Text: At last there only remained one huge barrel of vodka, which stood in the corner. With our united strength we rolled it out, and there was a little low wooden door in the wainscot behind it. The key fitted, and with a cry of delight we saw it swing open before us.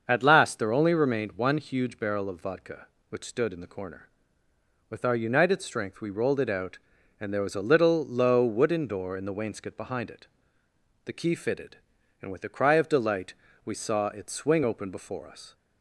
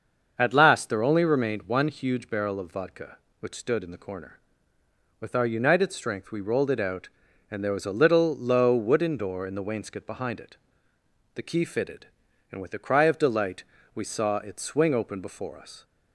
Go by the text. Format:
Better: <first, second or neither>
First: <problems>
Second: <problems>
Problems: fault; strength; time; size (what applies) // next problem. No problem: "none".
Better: neither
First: starts louder than the rest; until 1.0 s; 6.5 dB // pauses between "delight" and "we"; slight; at 13.3 s; 0.30 s long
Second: starts louder than the rest; until 1.3 s; 6.5 dB // pauses between "delight" and "we"; slight; at 13.6 s; 0.30 s long